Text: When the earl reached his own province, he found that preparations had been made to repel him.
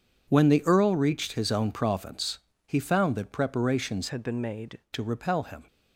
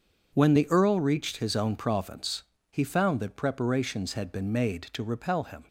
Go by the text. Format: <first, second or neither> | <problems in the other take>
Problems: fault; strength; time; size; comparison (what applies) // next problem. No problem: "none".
second | changes voice from "had" to "made"; from 4.0 to 4.7 s; 0.7 s long